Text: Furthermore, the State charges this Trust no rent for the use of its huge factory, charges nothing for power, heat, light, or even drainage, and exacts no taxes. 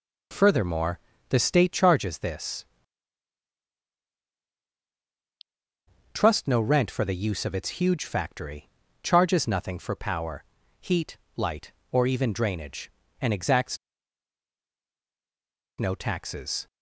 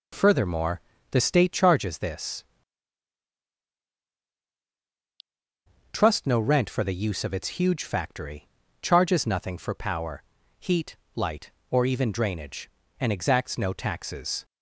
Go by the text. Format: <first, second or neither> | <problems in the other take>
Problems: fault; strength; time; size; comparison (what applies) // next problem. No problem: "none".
second | pauses between "this" and "Trust"; strong; at 2.6 s; 3.5 s long; strong in the second // pauses between "exacts" and "no"; strong; at 13.7 s; 2.0 s long